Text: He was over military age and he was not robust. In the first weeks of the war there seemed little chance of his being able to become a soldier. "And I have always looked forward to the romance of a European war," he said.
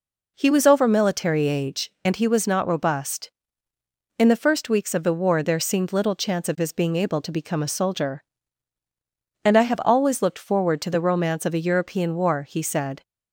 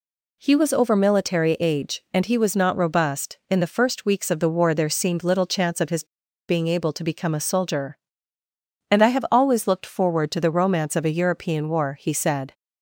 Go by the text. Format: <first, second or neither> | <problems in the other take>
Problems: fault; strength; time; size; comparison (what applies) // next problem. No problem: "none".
first | pauses between "his" and "being"; at 6.0 s; 0.44 s long